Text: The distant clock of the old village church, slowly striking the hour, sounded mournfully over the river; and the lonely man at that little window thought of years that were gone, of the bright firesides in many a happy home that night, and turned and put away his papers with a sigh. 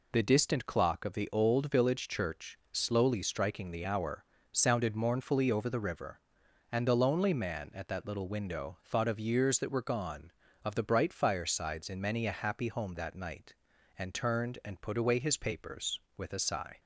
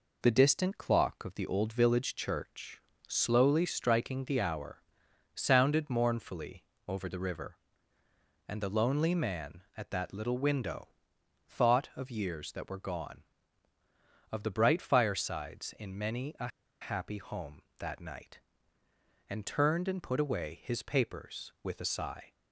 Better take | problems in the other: first | pauses between "mournfully" and "over"; slight; at 6.6 s; 0.24 s long // pauses between "window" and "thought"; noticeable; at 10.8 s; 0.58 s long // pauses between "a" and "happy"; slight; at 16.4 s; 0.31 s long

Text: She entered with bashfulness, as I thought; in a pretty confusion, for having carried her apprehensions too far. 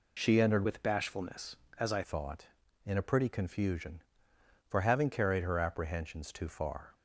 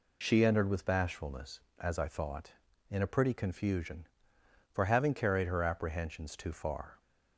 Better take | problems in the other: second | changes voice from "with" to "I"; from 0.6 to 2.0 s; 1.4 s long

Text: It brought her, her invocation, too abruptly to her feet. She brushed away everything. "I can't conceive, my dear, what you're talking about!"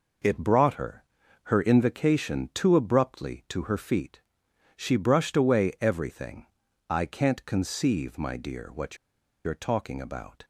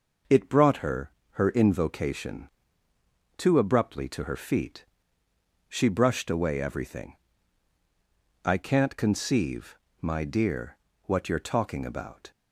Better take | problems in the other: second | pauses between "what" and "you're"; noticeable; at 8.9 s; 0.50 s long

